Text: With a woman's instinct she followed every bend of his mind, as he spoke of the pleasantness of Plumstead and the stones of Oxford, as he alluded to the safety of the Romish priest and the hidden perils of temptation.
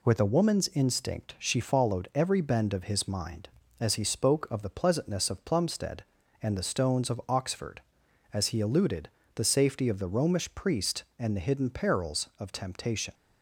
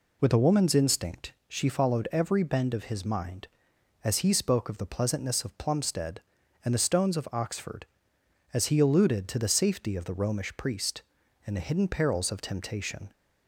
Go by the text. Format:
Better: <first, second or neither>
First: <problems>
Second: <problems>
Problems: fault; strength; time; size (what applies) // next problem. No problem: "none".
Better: second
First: skips "to"; at 9.2 s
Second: none